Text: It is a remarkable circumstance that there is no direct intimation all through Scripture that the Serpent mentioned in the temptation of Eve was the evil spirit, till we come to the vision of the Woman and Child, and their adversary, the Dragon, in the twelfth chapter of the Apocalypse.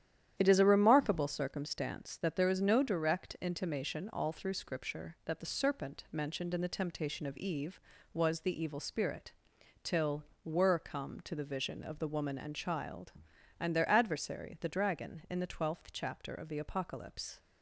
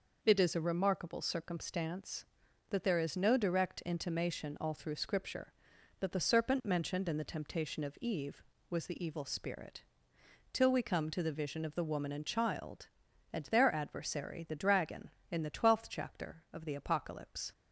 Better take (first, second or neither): second